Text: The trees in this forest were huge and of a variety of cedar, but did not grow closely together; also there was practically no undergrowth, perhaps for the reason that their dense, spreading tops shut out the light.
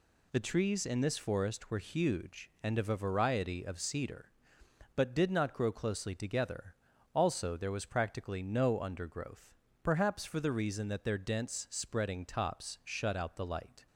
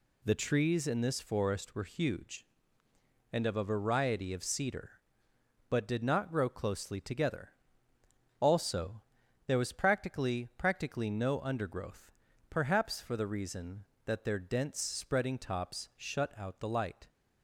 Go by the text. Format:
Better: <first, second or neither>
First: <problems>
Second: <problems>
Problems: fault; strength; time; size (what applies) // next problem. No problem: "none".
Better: first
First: none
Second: pauses between "also" and "there"; noticeable; at 9.0 s; 0.46 s long // says "practically" twice; at 10.5 s